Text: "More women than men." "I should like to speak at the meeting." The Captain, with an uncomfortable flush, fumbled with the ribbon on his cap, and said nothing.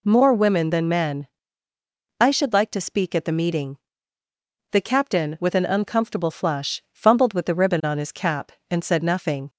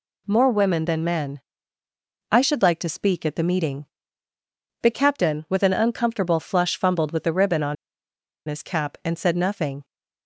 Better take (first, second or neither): first